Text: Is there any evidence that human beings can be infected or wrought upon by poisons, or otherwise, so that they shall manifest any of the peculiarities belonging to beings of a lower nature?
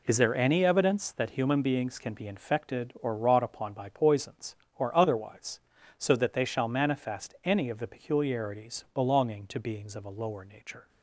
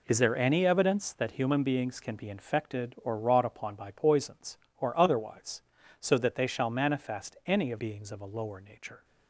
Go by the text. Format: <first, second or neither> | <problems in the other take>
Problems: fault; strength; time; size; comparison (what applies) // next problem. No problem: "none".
first | skips "the peculiarities belonging to"; at 7.7 s